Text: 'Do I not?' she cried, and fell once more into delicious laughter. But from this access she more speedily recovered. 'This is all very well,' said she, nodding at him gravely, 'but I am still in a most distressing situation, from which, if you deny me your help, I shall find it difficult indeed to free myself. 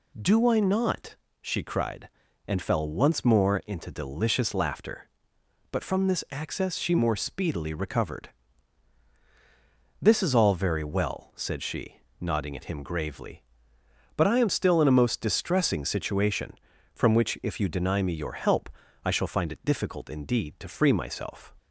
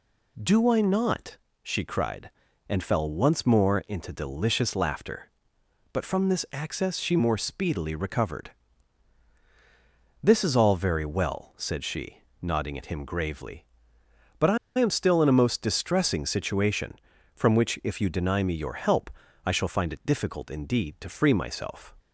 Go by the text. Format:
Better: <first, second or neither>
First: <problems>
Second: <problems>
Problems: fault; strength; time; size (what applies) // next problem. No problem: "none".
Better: first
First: none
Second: pauses between "I" and "am"; slight; at 14.5 s; 0.22 s long